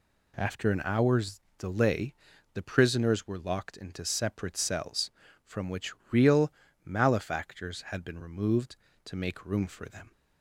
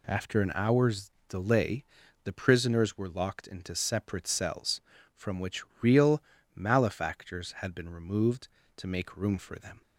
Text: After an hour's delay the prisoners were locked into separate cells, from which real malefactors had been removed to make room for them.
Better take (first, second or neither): neither